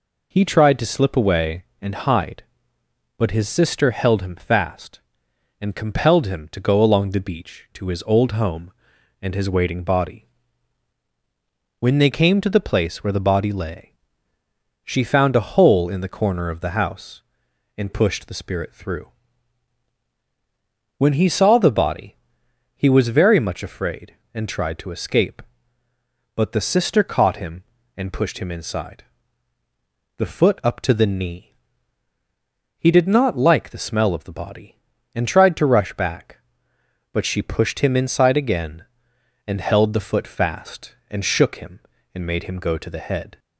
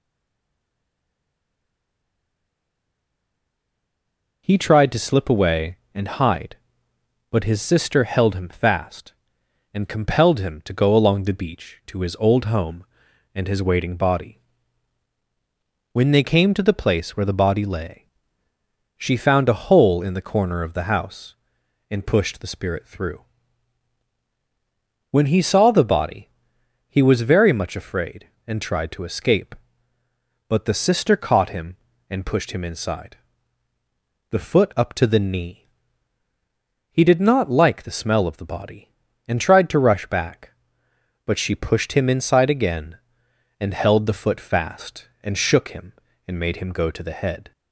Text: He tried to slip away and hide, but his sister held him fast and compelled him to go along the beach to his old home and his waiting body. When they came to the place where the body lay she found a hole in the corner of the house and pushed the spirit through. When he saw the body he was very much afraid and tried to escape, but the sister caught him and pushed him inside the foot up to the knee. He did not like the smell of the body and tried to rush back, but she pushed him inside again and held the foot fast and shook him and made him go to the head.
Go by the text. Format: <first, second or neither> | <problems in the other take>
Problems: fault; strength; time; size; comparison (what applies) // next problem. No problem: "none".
first | stays silent before the first word; strong; until 4.4 s; 4.4 s long // pauses between "lay" and "she"; noticeable; at 18.0 s; 0.96 s long; noticeable in the first // pauses between "body" and "he"; noticeable; at 26.2 s; 0.62 s long; noticeable in the first // pauses between "inside" and "the"; at 33.1 s; 1.1 s long; also in the first